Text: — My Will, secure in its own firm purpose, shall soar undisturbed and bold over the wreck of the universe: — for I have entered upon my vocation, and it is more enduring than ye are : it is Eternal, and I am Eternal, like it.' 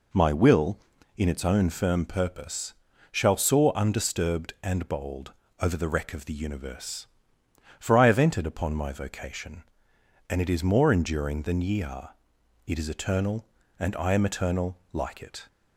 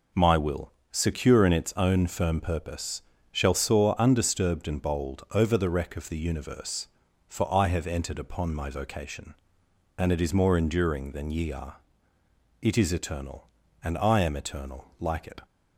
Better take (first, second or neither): second